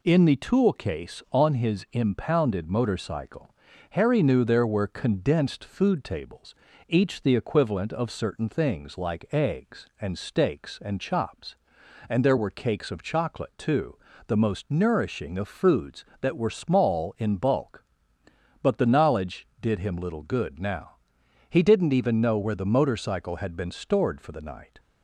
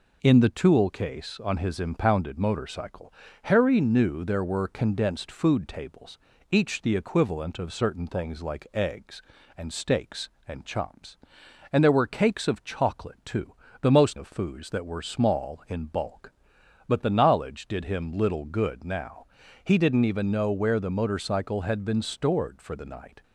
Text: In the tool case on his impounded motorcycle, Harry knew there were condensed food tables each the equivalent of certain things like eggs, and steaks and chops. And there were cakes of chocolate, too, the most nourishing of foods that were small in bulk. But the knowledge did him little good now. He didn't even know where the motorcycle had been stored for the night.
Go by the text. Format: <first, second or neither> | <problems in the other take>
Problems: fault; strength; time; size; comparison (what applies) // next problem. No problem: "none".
first | pauses between "tables" and "each"; slight; at 6.1 s; 0.34 s long; slight in the first // skips "nourishing"; at 14.1 s